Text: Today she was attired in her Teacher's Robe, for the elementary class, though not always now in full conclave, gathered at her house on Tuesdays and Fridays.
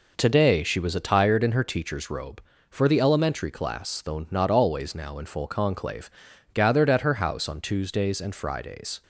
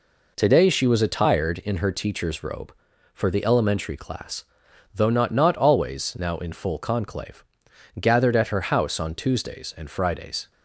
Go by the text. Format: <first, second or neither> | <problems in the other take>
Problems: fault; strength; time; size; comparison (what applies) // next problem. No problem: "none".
first | says "not" twice; at 5.3 s